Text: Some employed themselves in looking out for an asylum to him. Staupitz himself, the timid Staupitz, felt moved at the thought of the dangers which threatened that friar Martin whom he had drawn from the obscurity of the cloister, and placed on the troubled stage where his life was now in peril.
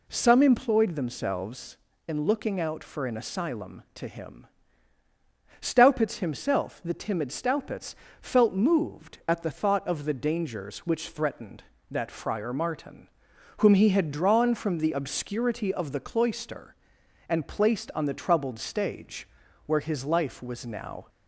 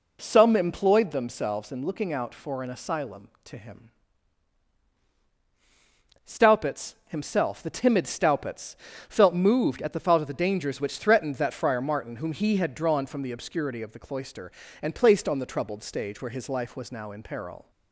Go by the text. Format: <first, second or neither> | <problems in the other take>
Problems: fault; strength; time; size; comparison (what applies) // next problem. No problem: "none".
second | pauses between "Martin" and "whom"; noticeable; at 13.0 s; 0.50 s long // pauses between "stage" and "where"; at 19.2 s; 0.40 s long // stops before "in peril"; at 21.0 s